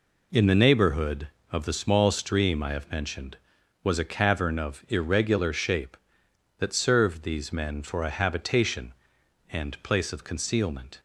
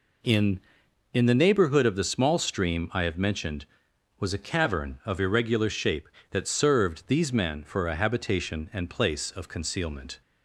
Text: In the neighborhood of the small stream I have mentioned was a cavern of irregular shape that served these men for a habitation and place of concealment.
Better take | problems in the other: first | says "In" twice; at 1.1 s

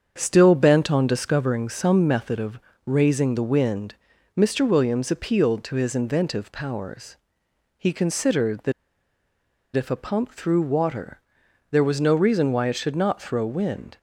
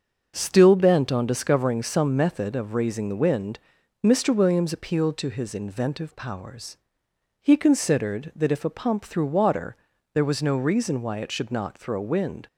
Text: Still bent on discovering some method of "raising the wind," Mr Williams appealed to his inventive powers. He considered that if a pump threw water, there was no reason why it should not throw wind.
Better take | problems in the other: second | starts louder than the rest; strong; until 1.1 s; 7 dB; also in the second // pauses between "of" and "raising"; slight; at 2.5 s; 0.28 s long // pauses between "that" and "if"; at 8.7 s; 1.0 s long

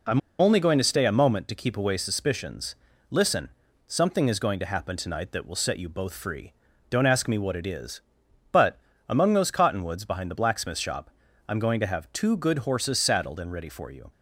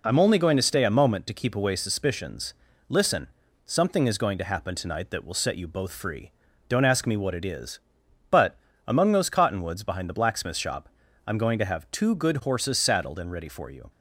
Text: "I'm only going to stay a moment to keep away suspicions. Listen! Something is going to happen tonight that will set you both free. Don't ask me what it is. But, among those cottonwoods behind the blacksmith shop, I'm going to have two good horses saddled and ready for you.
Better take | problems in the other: second | pauses between "I'm" and "only"; slight; at 0.2 s; 0.20 s long

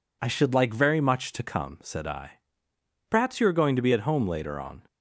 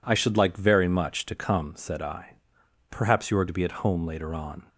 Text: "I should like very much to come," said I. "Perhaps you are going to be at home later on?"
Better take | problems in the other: first | skips "going"; at 3.4 s

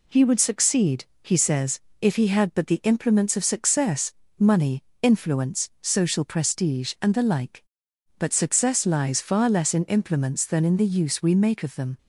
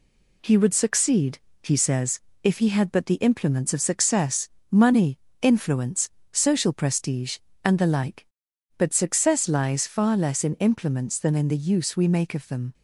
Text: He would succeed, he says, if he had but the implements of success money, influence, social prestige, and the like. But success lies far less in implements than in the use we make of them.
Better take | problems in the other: neither | pauses between "success" and "money"; slight; the same in both

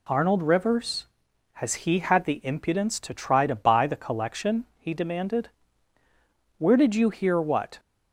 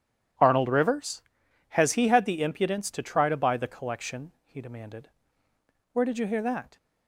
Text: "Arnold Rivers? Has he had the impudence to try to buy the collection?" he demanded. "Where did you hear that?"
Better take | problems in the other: second | says "what" for "that"; at 7.4 s

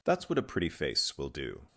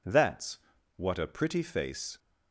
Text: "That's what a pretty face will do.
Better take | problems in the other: first | pauses between "That's" and "what"; at 0.5 s; 0.38 s long // stops before "will do"; at 2.1 s

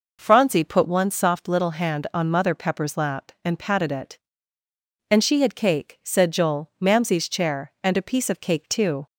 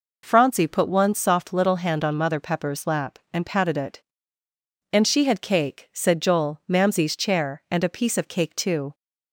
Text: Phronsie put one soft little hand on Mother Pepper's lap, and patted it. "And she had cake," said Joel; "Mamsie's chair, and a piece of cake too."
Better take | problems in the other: neither | none

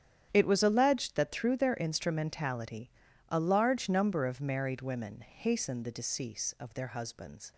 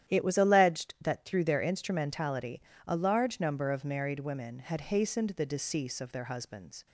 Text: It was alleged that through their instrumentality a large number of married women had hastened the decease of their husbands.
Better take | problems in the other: second | starts louder than the rest; strong; until 1.3 s; 9.5 dB; strong in the second // pauses between "instrumentality" and "a"; at 2.9 s; 0.40 s long; slight in the second // skips "had"; at 5.2 s

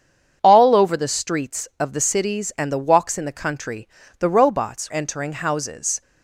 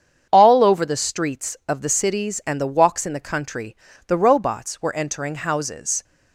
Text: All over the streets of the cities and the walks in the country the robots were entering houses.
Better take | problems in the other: second | starts louder than the rest; strong; until 1.4 s; 7.5 dB; strong in the second // pauses between "country" and "the"; slight; at 3.8 s; 0.30 s long; slight in the second // skips "were"; at 4.9 s

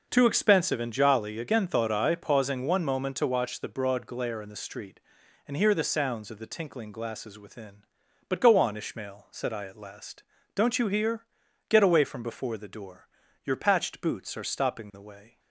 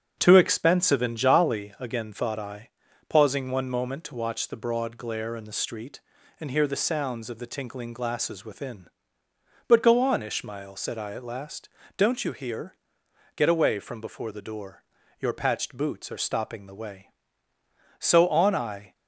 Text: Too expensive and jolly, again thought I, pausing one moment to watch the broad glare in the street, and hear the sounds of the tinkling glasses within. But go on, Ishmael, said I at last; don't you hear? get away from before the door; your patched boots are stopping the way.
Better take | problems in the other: first | starts louder than the rest; strong; until 1.1 s; 8 dB // goes on to say "So on I"; noticeable; from 18.0 s on; 0.95 s long

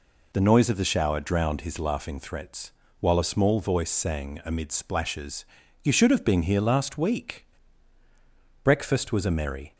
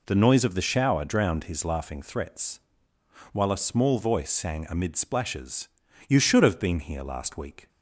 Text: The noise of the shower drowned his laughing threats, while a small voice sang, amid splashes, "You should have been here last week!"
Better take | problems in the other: second | goes on to say "Breakfast was a merry"; noticeable; from 8.6 s on; 1.1 s long

